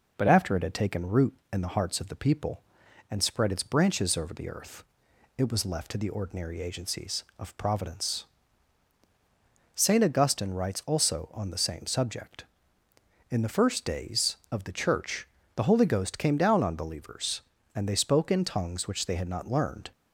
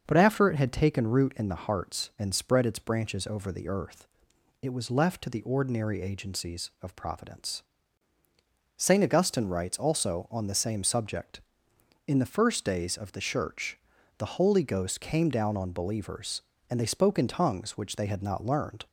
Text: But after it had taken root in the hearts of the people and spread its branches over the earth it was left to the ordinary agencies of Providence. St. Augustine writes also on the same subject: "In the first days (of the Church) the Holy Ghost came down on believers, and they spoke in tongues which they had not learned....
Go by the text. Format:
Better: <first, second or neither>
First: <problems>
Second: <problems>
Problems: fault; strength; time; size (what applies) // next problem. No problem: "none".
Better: first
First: pauses between "earth" and "it"; noticeable; at 4.8 s; 0.54 s long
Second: starts louder than the rest; until 1.0 s; 6.5 dB // skips "of the people"; at 2.1 s // pauses between "earth" and "it"; noticeable; at 4.0 s; 0.56 s long